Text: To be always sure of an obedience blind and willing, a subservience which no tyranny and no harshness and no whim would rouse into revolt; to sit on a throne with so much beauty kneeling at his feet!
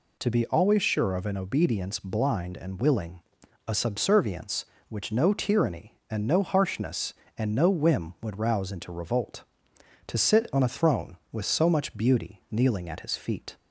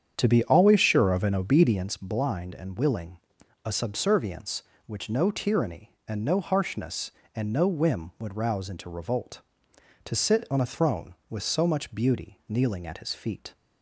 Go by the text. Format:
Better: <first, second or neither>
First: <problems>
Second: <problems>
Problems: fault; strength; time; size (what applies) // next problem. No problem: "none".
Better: first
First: none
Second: starts louder than the rest; strong; until 2.0 s; 8 dB